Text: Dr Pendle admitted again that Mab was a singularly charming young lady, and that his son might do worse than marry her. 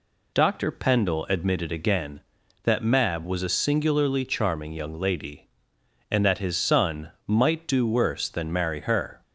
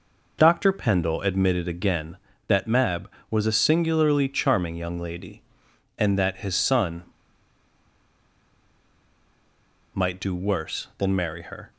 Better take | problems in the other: first | pauses between "son" and "might"; strong; at 7.0 s; 2.9 s long

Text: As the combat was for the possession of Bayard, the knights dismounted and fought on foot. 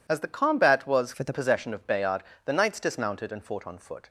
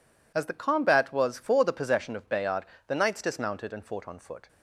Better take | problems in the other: second | changes voice from "for" to "the"; from 1.1 to 1.3 s; 0.2 s long

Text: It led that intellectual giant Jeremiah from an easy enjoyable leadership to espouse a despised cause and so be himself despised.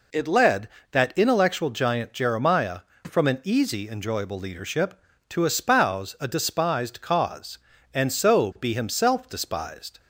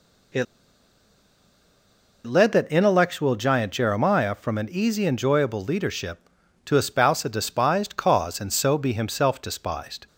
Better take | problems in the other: first | pauses between "It" and "led"; strong; at 0.4 s; 1.8 s long

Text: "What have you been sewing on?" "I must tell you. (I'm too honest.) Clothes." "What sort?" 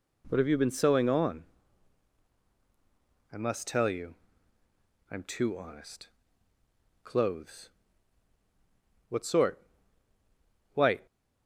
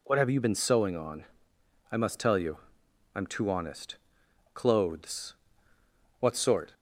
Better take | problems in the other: second | goes on to say "White"; slight; from 10.7 s on; 0.32 s long

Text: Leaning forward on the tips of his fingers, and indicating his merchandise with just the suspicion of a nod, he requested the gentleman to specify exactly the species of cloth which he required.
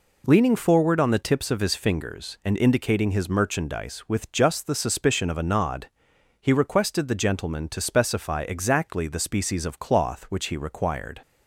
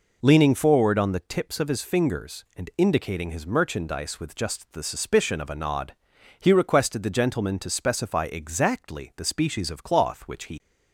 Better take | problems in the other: first | stops before "required"; at 10.5 s

